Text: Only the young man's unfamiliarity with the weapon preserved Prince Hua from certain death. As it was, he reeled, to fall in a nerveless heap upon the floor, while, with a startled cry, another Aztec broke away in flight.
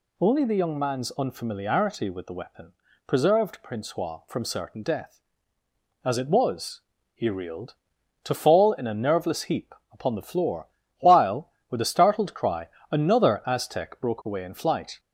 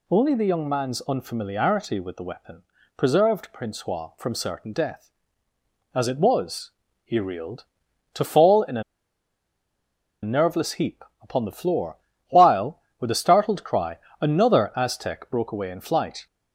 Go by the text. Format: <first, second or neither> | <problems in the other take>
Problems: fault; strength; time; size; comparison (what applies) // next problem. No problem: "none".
first | pauses between "weapon" and "preserved"; slight; at 2.6 s; 0.34 s long; slight in the first // pauses between "a" and "nerveless"; strong; at 8.8 s; 1.4 s long // pauses between "heap" and "upon"; slight; at 11.0 s; 0.18 s long; slight in the first